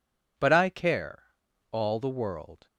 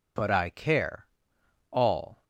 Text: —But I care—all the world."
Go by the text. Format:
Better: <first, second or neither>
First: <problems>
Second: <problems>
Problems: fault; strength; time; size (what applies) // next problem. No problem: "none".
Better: first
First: none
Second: stops before "the world"; at 2.2 s